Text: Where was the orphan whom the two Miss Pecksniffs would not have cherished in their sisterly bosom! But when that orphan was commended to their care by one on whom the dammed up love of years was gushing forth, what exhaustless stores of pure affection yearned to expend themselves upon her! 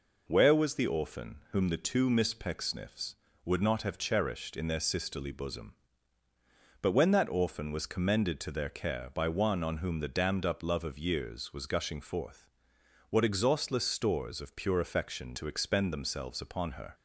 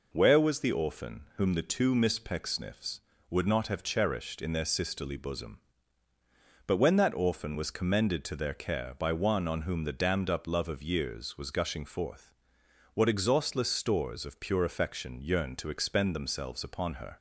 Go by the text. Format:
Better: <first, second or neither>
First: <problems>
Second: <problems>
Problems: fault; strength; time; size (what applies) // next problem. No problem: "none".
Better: second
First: skips "yearned"; at 15.3 s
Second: none